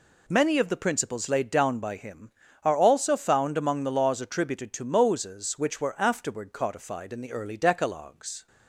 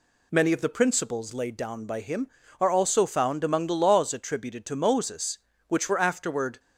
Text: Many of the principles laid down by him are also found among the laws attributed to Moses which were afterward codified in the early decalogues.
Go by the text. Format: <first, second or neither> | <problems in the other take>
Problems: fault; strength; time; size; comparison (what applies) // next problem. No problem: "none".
first | stops before "codified in the early decalogues"; at 6.5 s